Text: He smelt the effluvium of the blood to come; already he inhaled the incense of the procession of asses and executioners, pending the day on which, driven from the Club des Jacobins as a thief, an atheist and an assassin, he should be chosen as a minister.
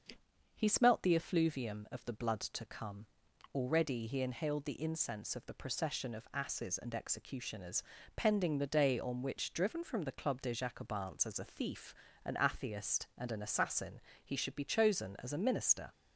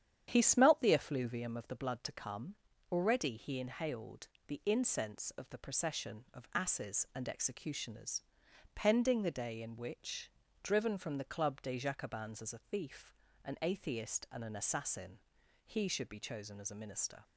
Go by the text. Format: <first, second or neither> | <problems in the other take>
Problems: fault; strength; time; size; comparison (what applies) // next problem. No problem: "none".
first | starts louder than the rest; strong; until 1.2 s; 9.5 dB; also in the first // pauses between "inhaled" and "the"; slight; at 4.2 s; 0.18 s long // says "in" for "on"; at 9.5 s